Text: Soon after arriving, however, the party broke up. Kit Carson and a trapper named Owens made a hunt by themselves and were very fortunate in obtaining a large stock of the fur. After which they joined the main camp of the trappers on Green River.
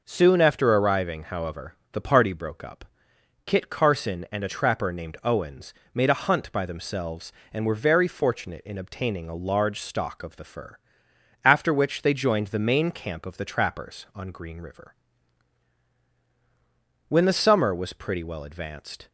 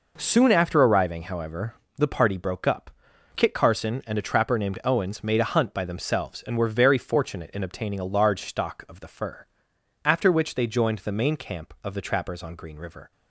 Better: second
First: pauses between "Owens" and "made"; slight; at 5.7 s; 0.20 s long // goes on to say "When the summer was pretty well advanced"; strong; from 17.0 s on; 2.0 s long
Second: none

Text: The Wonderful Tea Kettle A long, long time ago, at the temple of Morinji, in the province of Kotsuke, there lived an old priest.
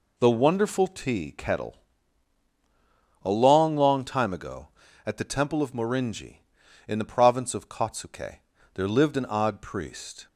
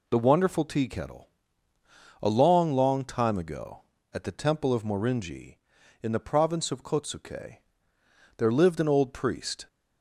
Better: second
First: pauses between "Kettle" and "A"; strong; at 1.7 s; 1.4 s long // says "odd" for "old"; at 9.2 s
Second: pauses between "Kettle" and "A"; noticeable; at 1.2 s; 0.96 s long

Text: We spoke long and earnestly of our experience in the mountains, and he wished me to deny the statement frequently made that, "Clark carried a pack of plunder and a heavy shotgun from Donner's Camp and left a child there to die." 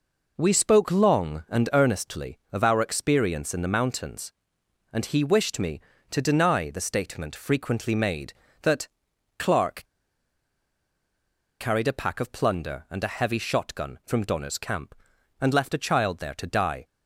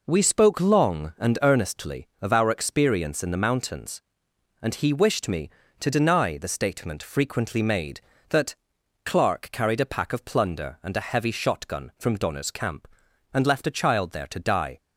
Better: second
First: pauses between "Clark" and "carried"; strong; at 9.8 s; 1.7 s long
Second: none

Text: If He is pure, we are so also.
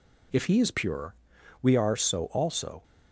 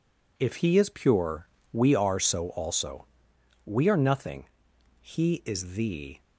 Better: first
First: none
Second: goes on to say "We are nothing He is the"; strong; from 3.6 s on; 2.5 s long

